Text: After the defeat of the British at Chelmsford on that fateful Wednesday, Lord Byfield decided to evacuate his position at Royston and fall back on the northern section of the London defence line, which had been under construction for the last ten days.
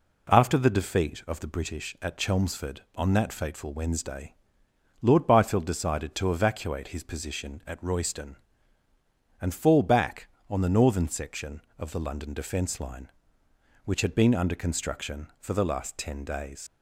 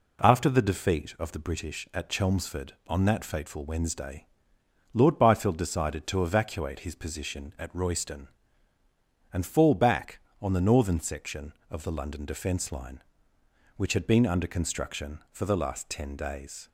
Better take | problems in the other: second | leaves "days" unfinished; at 16.6 s; 95 ms

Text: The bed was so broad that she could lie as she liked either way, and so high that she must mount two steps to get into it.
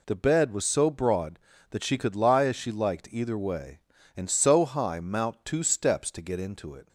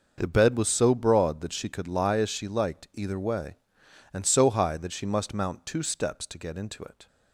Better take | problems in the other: second | skips "that she must"; at 4.9 s

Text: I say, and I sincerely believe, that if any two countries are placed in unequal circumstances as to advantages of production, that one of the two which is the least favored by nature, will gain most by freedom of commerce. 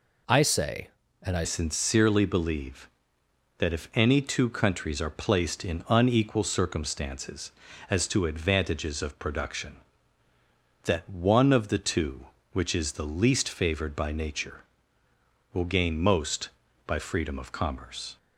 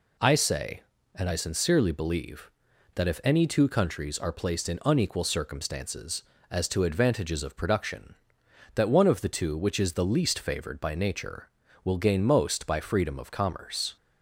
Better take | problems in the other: second | changes voice at "sincerely"; from 1.4 s on; 16.7 s long

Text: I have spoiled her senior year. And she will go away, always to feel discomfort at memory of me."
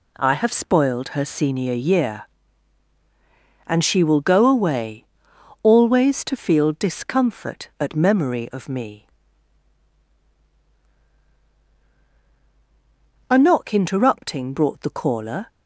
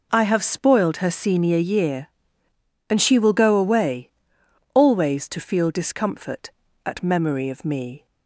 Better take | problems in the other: second | goes on to say "A knock interrupting brought the caller"; strong; from 13.2 s on; 2.2 s long

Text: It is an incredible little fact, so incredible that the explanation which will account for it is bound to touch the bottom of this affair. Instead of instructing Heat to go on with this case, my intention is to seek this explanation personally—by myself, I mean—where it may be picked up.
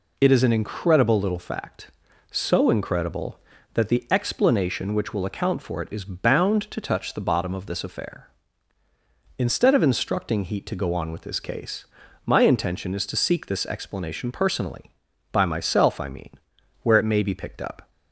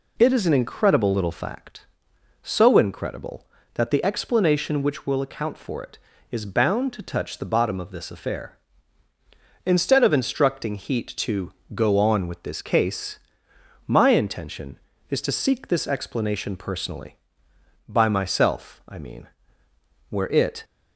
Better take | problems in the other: first | pauses between "to" and "go"; slight; at 11.5 s; 0.22 s long // stops before "may be picked up"; at 20.6 s

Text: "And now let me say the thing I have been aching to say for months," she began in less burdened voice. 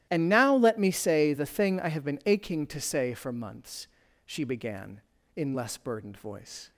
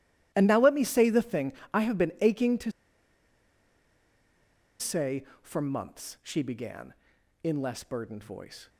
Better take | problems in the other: first | starts louder than the rest; strong; until 1.3 s; 14 dB; strong in the first // pauses between "thing" and "I"; slight; at 1.5 s; 0.22 s long // pauses between "to" and "say"; strong; at 2.7 s; 2.0 s long

